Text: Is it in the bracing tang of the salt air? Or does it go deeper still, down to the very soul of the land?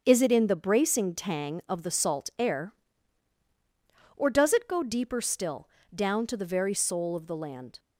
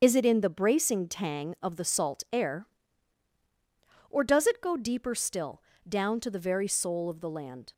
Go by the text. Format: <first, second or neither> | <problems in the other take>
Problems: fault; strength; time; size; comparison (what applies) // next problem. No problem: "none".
first | loses the start of "Is"; at 0.0 s; 40 ms // starts louder than the rest; until 1.0 s; 6.5 dB; also in the first